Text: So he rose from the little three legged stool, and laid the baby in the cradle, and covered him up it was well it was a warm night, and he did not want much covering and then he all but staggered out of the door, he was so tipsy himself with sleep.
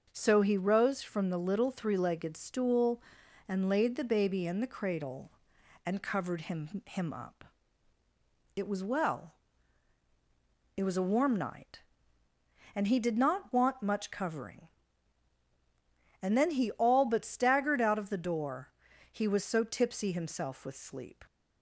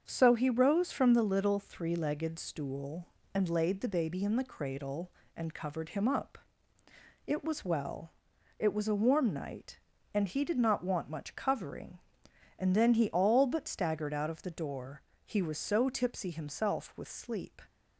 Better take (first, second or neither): second